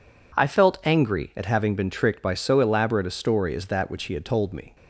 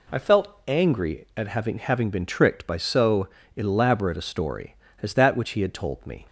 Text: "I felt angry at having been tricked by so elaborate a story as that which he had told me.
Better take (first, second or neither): first